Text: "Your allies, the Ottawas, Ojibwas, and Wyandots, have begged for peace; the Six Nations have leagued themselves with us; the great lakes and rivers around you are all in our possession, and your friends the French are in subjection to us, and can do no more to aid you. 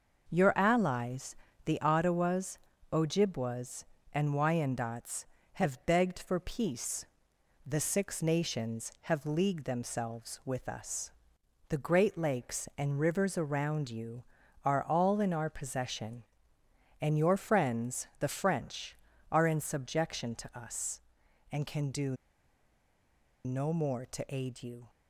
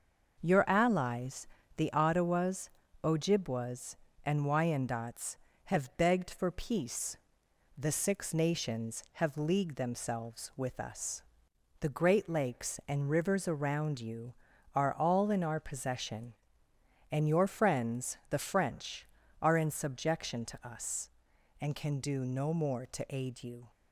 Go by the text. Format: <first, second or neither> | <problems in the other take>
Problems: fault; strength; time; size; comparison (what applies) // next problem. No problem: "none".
second | pauses between "do" and "no"; strong; at 22.1 s; 1.2 s long